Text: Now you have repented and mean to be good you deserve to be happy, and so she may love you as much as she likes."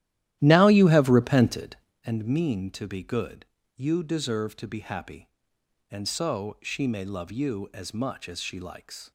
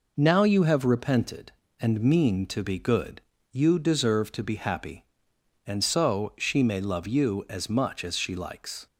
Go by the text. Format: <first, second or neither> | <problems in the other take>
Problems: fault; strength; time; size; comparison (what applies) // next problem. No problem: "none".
second | starts louder than the rest; strong; until 2.0 s; 13.5 dB // pauses between "good" and "you"; slight; at 3.4 s; 0.32 s long; slight in the second